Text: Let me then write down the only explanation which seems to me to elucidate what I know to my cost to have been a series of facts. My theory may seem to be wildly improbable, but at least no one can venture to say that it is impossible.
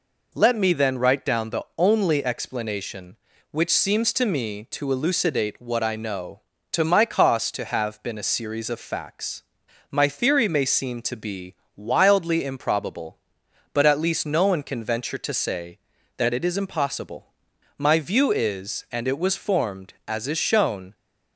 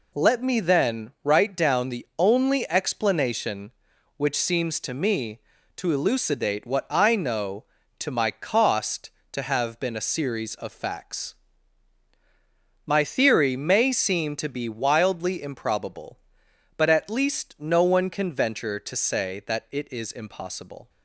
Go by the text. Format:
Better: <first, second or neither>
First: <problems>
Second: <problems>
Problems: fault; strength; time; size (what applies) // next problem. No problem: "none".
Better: second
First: pauses between "be" and "wildly"; slight; at 11.5 s; 0.22 s long // goes on to say "My view is and it was formed as is shown"; strong; from 17.7 s on; 3.1 s long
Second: none